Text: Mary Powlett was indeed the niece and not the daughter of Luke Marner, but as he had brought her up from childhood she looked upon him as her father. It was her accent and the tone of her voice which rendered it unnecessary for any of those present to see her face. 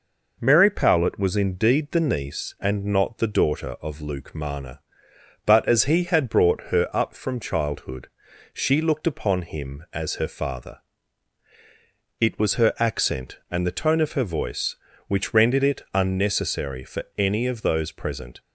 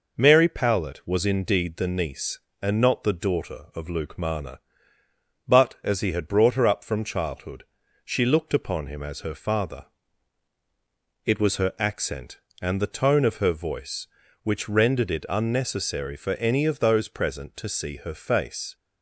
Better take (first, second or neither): second